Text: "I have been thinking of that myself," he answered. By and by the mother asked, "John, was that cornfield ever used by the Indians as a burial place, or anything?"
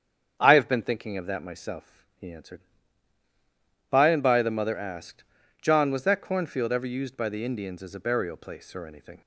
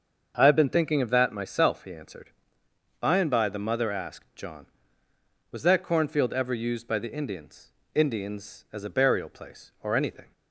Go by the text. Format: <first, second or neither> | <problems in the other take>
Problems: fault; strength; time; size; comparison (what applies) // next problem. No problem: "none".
first | starts louder than the rest; until 1.3 s; 6.5 dB; strong in the first // says "Indians" twice; at 7.9 s